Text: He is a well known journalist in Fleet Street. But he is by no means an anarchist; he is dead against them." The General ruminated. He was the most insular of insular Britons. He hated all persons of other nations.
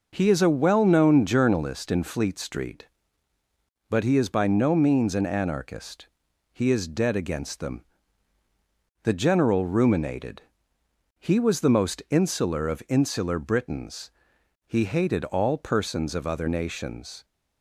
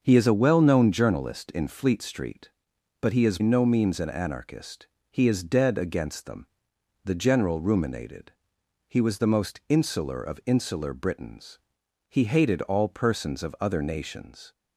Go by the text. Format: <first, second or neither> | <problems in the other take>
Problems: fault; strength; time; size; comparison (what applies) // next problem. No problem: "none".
first | starts louder than the rest; until 1.0 s; 6.5 dB // skips "by"; at 3.4 s